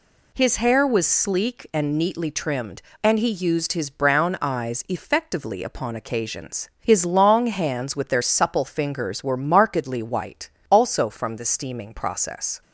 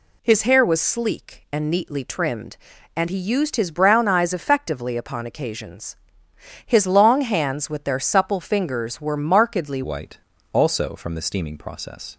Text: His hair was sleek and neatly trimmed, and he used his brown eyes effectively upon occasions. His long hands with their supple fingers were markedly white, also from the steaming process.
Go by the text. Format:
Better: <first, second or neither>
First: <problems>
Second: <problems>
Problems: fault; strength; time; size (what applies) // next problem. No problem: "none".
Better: first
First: none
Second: changes voice at "white"; from 9.8 s on; 2.3 s long